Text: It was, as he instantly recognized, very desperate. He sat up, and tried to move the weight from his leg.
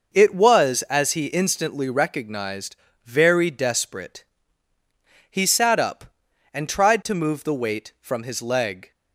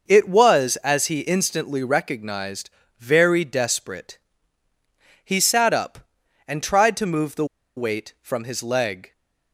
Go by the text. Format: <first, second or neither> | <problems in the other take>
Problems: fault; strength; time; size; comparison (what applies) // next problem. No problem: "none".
first | pauses between "the" and "weight"; slight; at 7.4 s; 0.32 s long